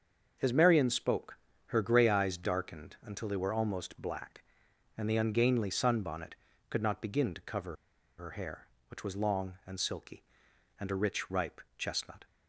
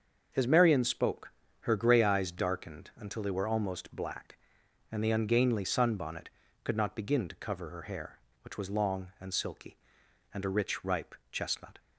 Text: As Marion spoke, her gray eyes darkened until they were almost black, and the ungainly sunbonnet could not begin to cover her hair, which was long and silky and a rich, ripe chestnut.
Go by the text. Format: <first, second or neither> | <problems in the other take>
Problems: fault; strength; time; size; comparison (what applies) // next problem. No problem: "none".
second | starts louder than the rest; until 1.7 s; 6.5 dB; also in the second // pauses between "cover" and "her"; at 7.7 s; 0.44 s long // pauses between "ripe" and "chestnut"; slight; at 11.6 s; 0.16 s long; slight in the second